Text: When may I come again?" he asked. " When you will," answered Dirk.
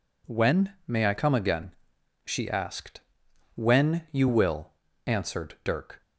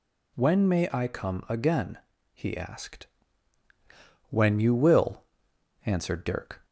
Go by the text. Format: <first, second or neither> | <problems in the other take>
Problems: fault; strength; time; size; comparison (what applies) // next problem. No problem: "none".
second | says "she" for "he"; at 2.2 s